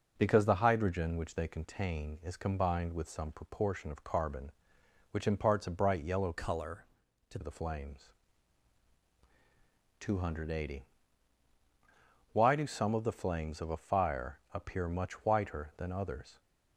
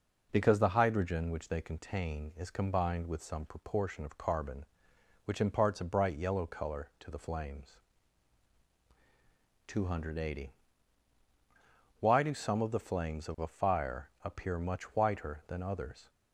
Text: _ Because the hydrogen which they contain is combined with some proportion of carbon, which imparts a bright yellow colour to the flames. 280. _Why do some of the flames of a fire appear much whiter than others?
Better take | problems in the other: second | changes voice from "colour" to "to"; from 6.3 to 7.3 s; 1.0 s long

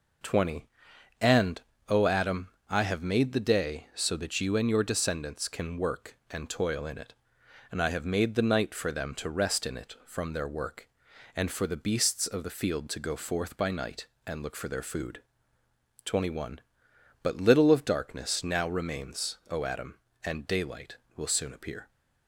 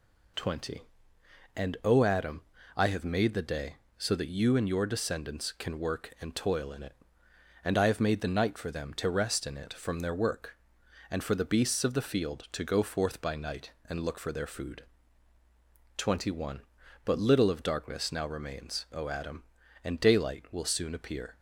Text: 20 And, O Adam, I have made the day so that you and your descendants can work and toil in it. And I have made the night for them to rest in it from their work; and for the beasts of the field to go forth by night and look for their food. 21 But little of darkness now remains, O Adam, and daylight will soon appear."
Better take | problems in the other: neither | none

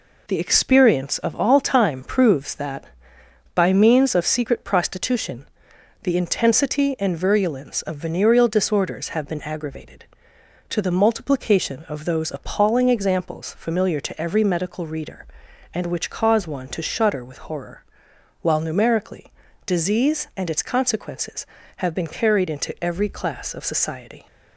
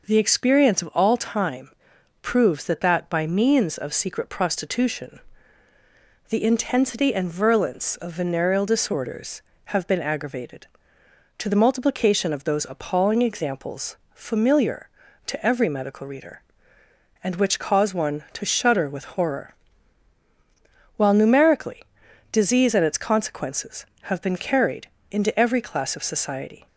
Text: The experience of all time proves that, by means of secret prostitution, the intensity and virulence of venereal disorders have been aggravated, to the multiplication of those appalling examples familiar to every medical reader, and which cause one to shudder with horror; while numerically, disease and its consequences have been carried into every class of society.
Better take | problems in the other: first | pauses between "time" and "proves"; noticeable; at 1.7 s; 0.50 s long // says "that" twice; at 2.8 s // pauses between "examples" and "familiar"; slight; at 13.9 s; 0.16 s long // pauses between "carried" and "into"; slight; at 24.8 s; 0.22 s long

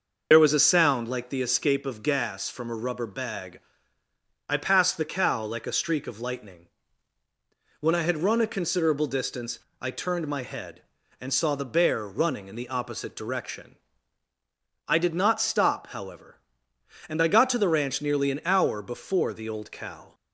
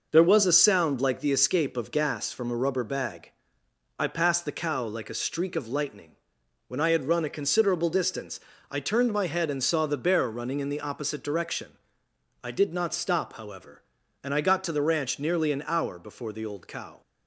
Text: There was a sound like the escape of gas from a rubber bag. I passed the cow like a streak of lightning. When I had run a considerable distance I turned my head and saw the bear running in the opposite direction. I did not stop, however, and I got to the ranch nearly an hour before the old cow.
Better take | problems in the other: second | loses the start of "There"; at 0.3 s; 70 ms // pauses between "distance" and "I"; slight; at 9.5 s; 0.24 s long; slight in the second

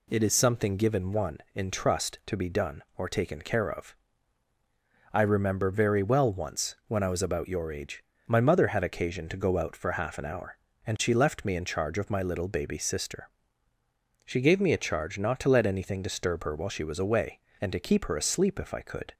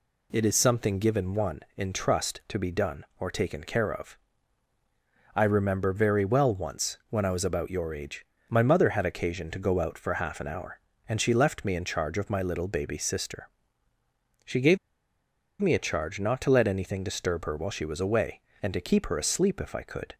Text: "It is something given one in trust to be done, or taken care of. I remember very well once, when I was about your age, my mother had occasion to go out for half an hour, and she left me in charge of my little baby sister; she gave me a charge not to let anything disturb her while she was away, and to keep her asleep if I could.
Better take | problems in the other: first | pauses between "gave" and "me"; noticeable; at 14.7 s; 0.82 s long

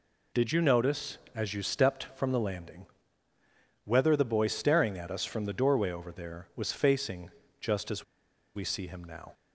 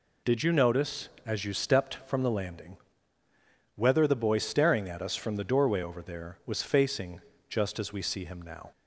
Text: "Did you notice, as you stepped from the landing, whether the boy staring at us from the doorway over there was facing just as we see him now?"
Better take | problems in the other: second | pauses between "facing" and "just"; slight; at 7.2 s; 0.32 s long; slight in the second // pauses between "as" and "we"; noticeable; at 8.0 s; 0.52 s long

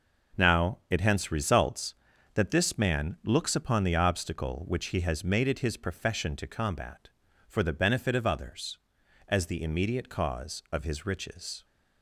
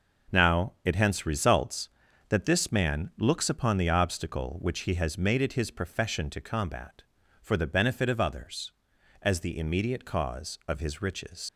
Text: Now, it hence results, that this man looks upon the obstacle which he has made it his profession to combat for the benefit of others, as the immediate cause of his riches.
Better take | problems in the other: first | leaves "riches" unfinished; at 11.4 s; 115 ms

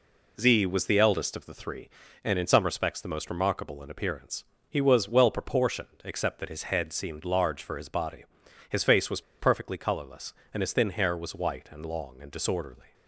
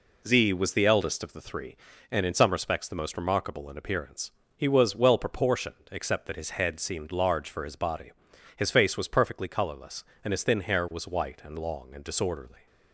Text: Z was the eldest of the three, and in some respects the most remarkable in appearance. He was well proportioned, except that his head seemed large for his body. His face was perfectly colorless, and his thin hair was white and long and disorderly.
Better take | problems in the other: second | pauses between "was" and "perfectly"; slight; at 9.2 s; 0.18 s long

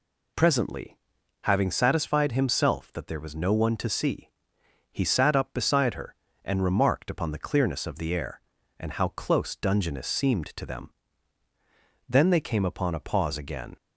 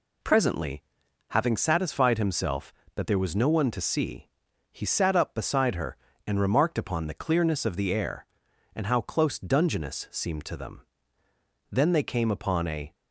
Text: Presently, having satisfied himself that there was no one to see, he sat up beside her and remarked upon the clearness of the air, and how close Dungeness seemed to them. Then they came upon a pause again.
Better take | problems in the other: first | stops before "pause again"; at 12.9 s

